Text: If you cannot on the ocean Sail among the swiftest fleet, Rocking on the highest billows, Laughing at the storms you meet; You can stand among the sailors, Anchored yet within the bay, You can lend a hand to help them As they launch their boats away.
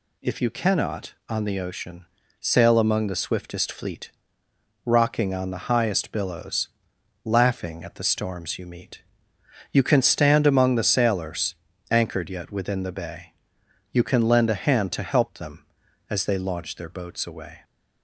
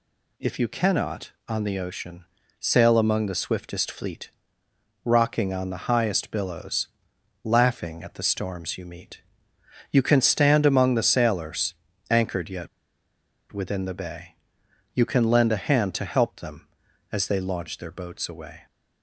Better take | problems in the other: first | pauses between "ocean" and "Sail"; slight; at 2.2 s; 0.34 s long; slight in the first // pauses between "yet" and "within"; noticeable; at 12.6 s; 0.83 s long

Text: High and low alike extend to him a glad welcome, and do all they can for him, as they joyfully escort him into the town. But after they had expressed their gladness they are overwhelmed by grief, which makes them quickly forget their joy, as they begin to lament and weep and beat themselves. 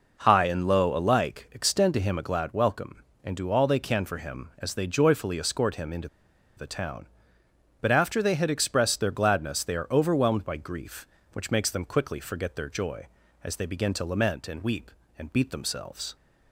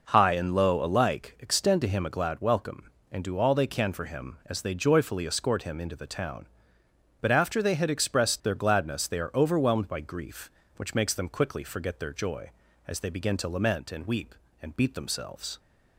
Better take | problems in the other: second | pauses between "into" and "the"; noticeable; at 6.0 s; 0.49 s long

